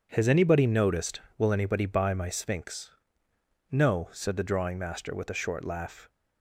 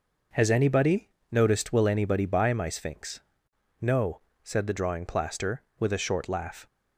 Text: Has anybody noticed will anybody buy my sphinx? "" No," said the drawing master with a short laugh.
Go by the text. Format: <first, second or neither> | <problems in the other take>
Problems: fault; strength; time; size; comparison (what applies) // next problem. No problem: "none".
first | pauses between "anybody" and "noticed"; slight; at 1.0 s; 0.20 s long // says "plaster" for "master"; at 5.0 s